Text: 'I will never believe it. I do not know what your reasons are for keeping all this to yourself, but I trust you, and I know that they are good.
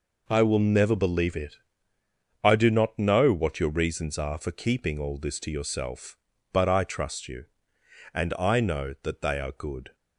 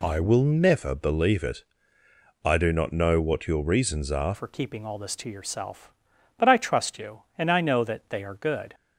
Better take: first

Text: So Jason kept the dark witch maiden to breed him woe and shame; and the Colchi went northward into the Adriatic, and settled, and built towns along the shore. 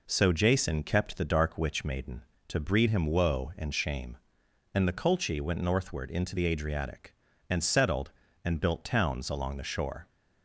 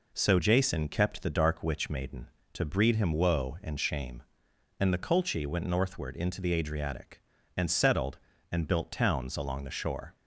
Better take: neither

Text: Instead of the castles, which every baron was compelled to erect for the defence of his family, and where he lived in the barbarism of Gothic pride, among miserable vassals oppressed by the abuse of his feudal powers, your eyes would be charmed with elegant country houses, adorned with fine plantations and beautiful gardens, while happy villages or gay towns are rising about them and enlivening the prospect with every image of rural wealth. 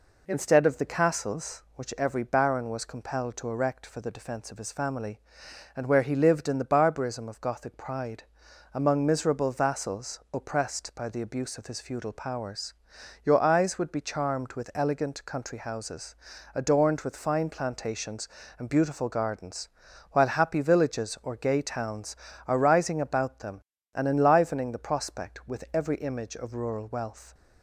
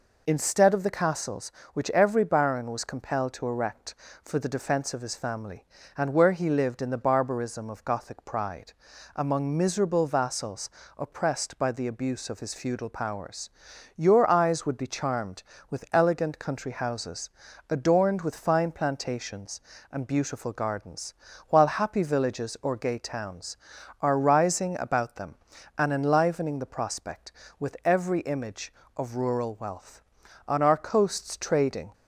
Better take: first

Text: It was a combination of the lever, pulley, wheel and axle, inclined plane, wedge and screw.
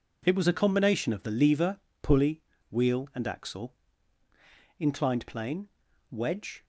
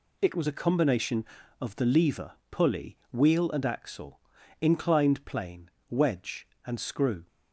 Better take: second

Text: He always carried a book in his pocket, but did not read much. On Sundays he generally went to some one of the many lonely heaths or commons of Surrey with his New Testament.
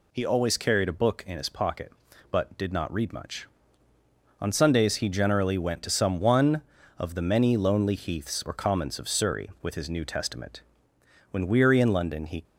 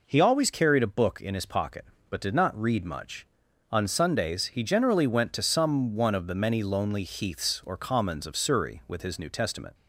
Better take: second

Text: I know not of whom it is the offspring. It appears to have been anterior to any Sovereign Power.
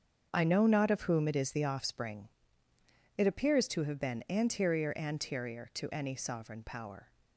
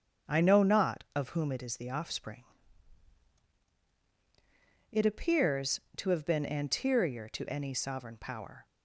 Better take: second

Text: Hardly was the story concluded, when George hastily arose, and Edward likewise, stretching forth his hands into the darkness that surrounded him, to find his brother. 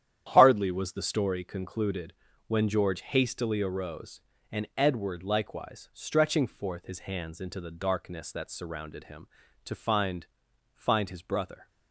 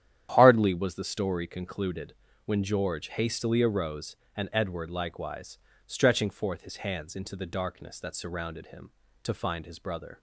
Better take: second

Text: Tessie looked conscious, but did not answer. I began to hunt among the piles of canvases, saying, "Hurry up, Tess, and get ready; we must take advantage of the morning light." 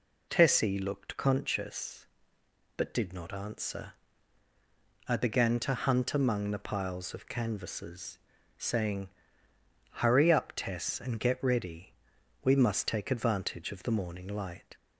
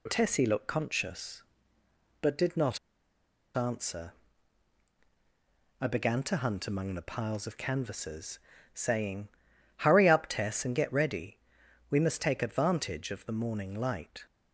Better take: first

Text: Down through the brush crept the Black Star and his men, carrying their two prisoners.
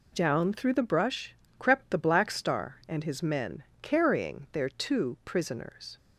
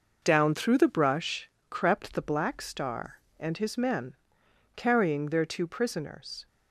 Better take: neither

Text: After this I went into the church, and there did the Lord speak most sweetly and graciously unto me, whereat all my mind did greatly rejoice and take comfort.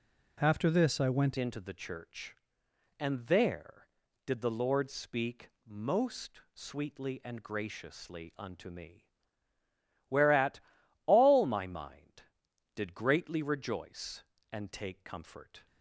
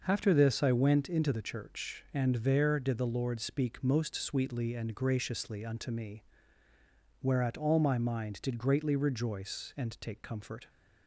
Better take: second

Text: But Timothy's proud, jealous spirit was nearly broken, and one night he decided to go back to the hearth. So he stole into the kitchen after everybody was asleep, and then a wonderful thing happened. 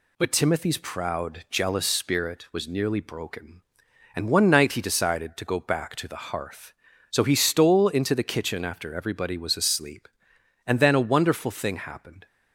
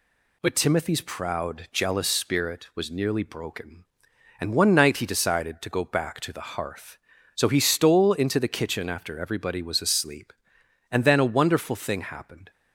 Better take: neither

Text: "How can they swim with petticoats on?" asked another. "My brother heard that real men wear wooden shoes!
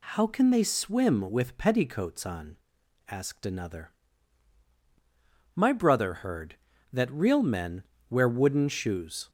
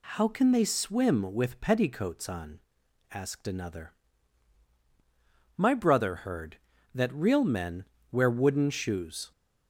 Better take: neither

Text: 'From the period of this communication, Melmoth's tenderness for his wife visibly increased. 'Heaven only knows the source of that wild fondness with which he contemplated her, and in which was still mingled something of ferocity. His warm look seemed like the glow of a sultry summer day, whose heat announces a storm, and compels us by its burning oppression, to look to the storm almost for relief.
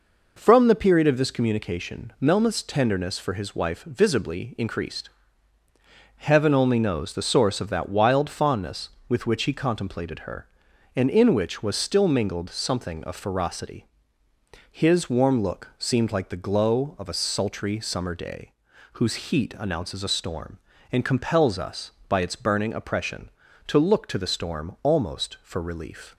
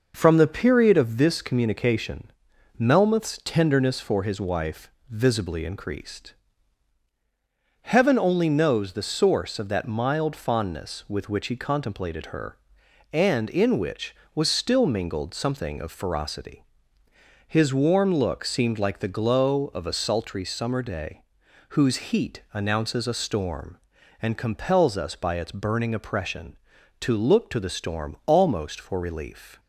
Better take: first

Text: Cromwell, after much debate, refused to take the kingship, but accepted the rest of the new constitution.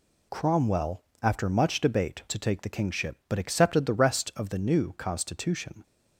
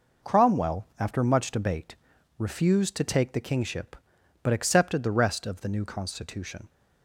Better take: second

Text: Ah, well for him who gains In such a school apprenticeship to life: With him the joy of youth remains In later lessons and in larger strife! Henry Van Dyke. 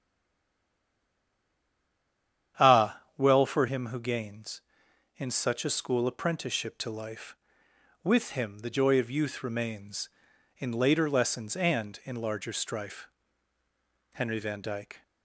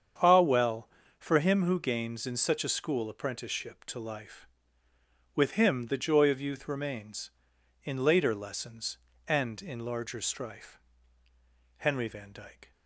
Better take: second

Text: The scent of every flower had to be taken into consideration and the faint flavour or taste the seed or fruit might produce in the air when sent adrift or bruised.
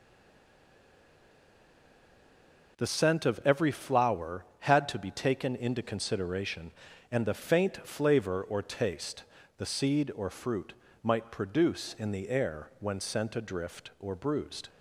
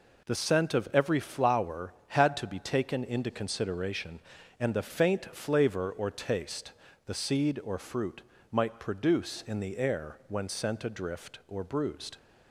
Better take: second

